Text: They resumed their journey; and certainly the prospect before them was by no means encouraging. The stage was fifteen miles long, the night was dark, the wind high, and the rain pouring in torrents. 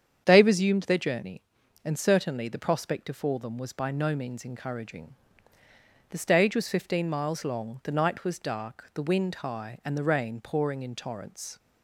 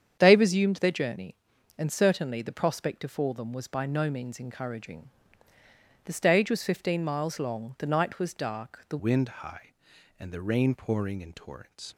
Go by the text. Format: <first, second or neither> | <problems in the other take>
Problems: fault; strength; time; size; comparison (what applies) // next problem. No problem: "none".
first | starts louder than the rest; strong; until 1.2 s; 8 dB; strong in the first // changes voice at "wind"; from 8.9 s on; 3.0 s long